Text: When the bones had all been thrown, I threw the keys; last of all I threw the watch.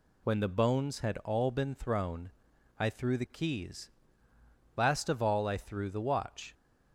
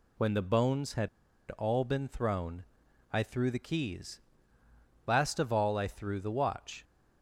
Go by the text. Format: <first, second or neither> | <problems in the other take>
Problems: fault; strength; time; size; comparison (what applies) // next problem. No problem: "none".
first | pauses between "had" and "all"; at 1.0 s; 0.42 s long